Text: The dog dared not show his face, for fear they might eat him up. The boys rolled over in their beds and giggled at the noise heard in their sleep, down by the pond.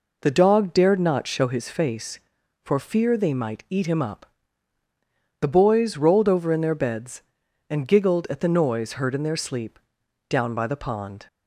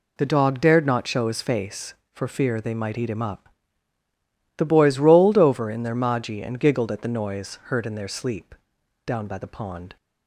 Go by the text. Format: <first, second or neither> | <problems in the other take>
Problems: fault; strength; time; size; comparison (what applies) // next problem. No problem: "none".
first | says "maji" for "beds"; at 5.9 s